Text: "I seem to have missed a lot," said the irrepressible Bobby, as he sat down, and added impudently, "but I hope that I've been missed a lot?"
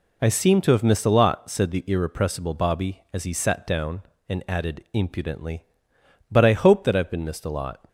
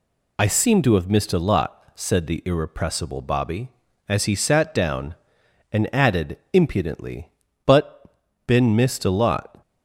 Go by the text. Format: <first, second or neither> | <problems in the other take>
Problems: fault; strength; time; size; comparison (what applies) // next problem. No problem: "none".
first | pauses between "added" and "impudently"; slight; at 6.3 s; 0.16 s long // skips "I hope that I've"; at 8.2 s